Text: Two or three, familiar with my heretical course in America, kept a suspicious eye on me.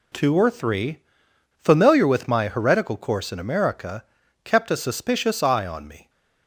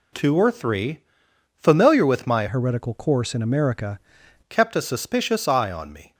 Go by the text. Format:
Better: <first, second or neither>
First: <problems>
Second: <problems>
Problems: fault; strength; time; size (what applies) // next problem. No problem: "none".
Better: first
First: none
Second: changes voice from "heretical" to "America"; from 2.4 to 3.9 s; 1.5 s long